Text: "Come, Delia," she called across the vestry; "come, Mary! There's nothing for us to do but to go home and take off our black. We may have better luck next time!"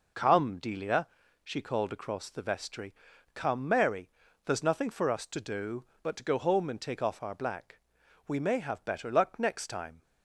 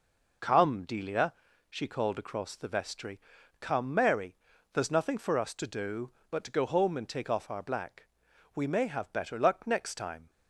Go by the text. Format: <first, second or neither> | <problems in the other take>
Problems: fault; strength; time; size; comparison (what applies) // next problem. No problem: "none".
neither | none